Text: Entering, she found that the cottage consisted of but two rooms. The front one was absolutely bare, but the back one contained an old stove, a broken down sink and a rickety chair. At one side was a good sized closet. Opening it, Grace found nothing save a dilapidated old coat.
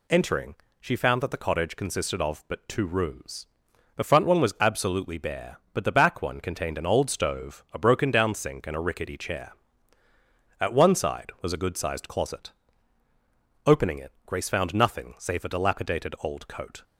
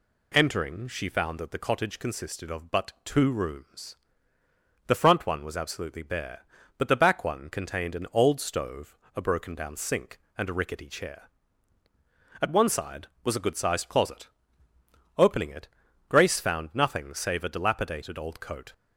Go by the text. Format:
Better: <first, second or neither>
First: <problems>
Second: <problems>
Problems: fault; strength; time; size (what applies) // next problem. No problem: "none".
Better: neither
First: none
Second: none